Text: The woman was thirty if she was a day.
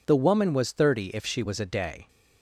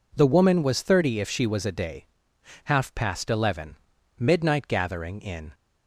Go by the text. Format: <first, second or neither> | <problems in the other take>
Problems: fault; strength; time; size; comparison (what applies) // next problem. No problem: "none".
first | goes on to say "Half past eleven Midnight gathering in"; strong; from 2.6 s on; 2.8 s long